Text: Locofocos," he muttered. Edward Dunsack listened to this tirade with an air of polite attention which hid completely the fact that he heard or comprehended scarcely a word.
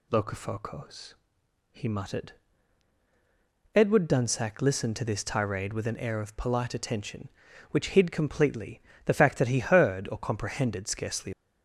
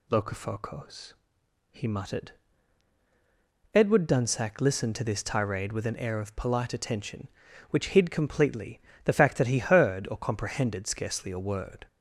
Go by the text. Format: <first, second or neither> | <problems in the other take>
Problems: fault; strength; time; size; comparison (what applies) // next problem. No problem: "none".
second | pauses between "completely" and "the"; slight; at 8.7 s; 0.24 s long; slight in the second // stops before "a word"; at 11.3 s